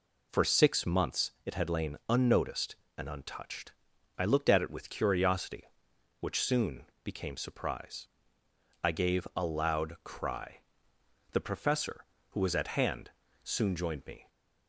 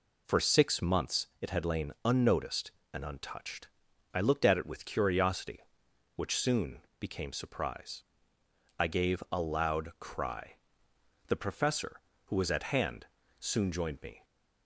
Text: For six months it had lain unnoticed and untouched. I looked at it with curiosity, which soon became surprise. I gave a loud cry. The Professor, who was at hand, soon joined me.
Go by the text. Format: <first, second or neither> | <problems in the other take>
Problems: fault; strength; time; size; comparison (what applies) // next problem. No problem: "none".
neither | pauses between "soon" and "became"; slight; the same in both